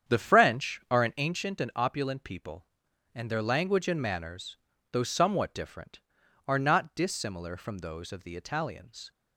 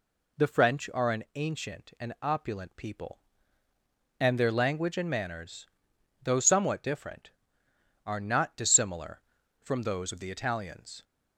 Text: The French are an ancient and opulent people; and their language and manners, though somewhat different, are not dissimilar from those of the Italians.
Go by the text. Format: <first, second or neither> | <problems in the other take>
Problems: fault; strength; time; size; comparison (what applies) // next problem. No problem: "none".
second | starts louder than the rest; strong; until 1.3 s; 8.5 dB